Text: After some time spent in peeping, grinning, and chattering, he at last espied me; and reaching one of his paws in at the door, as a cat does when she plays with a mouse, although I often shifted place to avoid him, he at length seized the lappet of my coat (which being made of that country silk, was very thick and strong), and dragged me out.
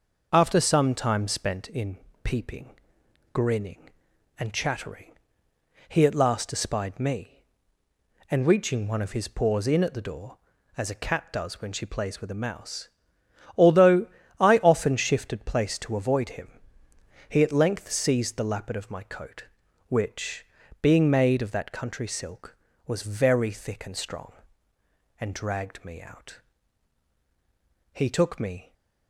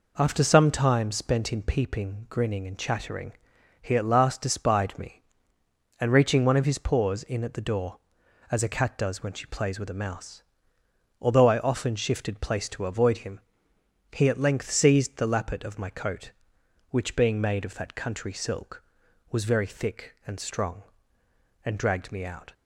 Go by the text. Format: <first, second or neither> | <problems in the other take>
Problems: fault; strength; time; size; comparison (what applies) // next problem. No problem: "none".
second | pauses between "in" and "peeping"; slight; at 1.9 s; 0.26 s long // pauses between "although" and "I"; slight; at 14.0 s; 0.30 s long // pauses between "which" and "being"; slight; at 20.4 s; 0.36 s long // goes on to say "He took me"; noticeable; from 27.9 s on; 0.80 s long